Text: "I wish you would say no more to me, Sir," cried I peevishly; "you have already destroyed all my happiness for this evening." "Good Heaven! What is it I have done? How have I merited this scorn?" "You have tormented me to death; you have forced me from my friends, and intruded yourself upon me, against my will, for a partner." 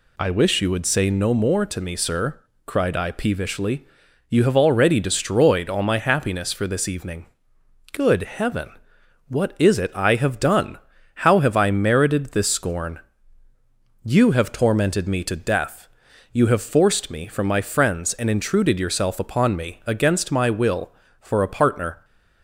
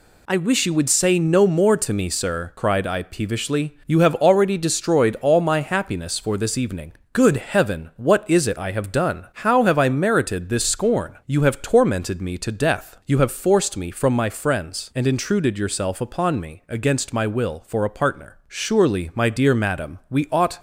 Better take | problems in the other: first | goes on to say "Surely my dear Madam we ought"; strong; from 18.4 s on; 2.1 s long

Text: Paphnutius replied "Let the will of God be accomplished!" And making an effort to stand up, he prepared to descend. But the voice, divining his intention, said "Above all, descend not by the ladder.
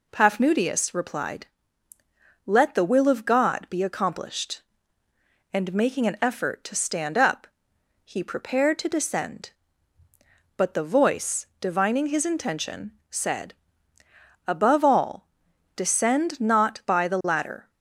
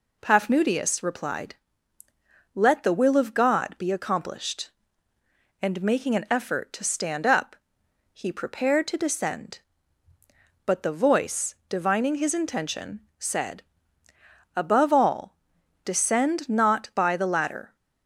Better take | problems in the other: neither | pauses between "replied" and "Let"; the same in both // pauses between "said" and "Above"; noticeable; the same in both

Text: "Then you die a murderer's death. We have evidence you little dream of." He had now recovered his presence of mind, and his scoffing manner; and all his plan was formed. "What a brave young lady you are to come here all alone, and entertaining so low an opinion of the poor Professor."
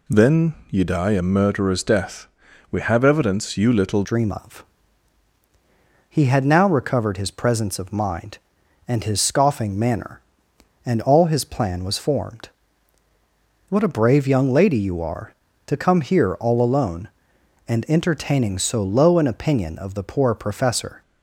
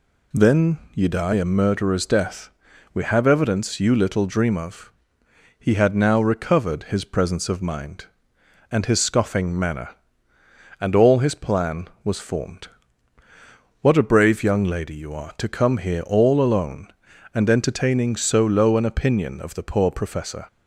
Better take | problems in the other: second | pauses between "Then" and "you"; slight; at 0.5 s; 0.16 s long; slight in the second // changes voice at "dream"; from 4.0 s on; 17.0 s long

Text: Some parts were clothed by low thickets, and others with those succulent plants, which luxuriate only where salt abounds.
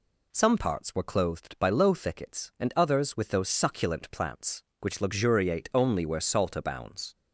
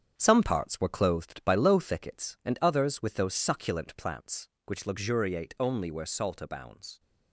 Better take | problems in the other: first | gets quieter; throughout; 6.5 dB

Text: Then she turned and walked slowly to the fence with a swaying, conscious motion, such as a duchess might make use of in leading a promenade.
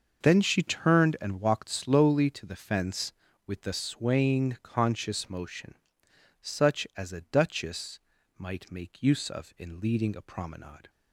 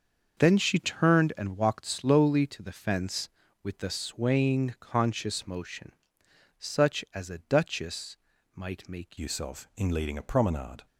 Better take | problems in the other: first | starts louder than the rest; until 1.4 s; 6.5 dB; also in the first // pauses between "duchess" and "might"; at 8.1 s; 0.38 s long; also in the first // changes voice at "use"; from 9.1 s on; 1.7 s long

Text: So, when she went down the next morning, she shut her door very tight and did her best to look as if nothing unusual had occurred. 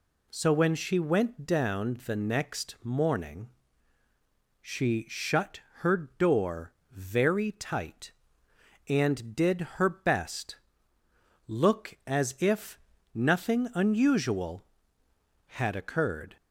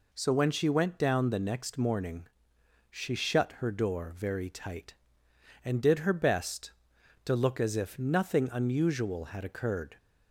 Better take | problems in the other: second | pauses between "shut" and "her"; slight; at 5.6 s; 0.20 s long // pauses between "door" and "very"; slight; at 6.7 s; 0.18 s long // pauses between "did" and "her"; slight; at 9.6 s; 0.16 s long // skips "to"; at 11.0 s // pauses between "if" and "nothing"; slight; at 12.7 s; 0.36 s long

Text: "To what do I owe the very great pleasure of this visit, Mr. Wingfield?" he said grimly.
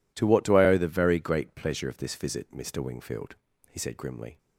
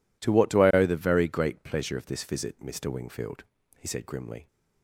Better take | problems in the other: neither | none

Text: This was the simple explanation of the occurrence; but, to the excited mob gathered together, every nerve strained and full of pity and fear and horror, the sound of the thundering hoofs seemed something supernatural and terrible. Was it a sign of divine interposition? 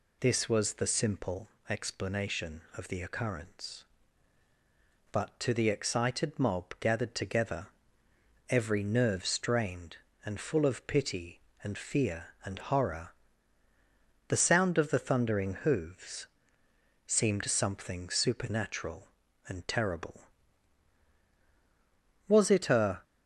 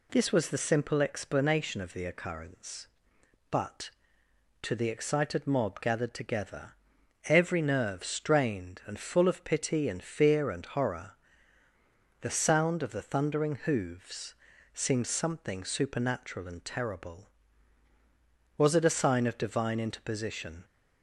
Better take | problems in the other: second | pauses between "simple" and "explanation"; slight; at 1.4 s; 0.20 s long // pauses between "hoofs" and "seemed"; noticeable; at 16.2 s; 0.80 s long; also in the second // stops before "sign of divine interposition"; at 23.0 s

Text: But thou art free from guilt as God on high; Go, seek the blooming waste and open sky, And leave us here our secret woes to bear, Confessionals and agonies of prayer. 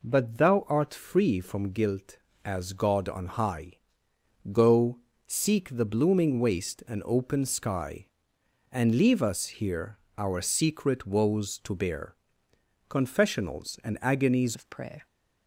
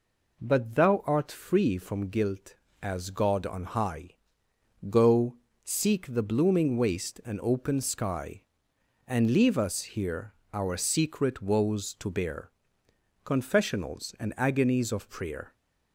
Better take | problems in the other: second | pauses between "here" and "our"; slight; at 9.9 s; 0.20 s long; slight in the second // changes voice at "of"; from 14.5 s on; 0.5 s long

